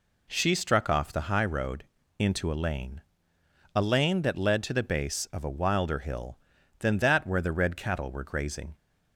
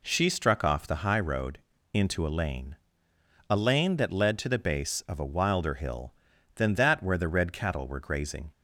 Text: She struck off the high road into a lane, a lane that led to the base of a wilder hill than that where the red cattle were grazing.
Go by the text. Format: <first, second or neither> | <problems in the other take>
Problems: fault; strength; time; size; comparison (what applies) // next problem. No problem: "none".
neither | pauses between "road" and "into"; slight; the same in both